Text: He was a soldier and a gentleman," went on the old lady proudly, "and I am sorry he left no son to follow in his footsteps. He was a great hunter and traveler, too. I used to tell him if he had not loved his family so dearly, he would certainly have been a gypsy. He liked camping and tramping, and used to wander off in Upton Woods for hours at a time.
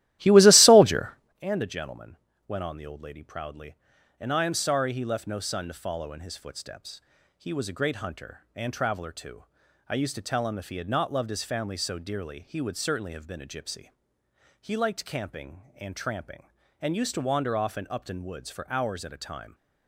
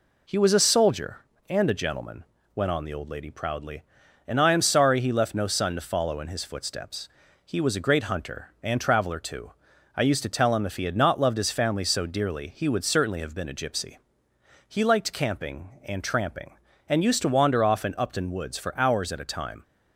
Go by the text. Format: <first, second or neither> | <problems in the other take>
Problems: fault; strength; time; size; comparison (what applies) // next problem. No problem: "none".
second | starts louder than the rest; strong; until 1.4 s; 15 dB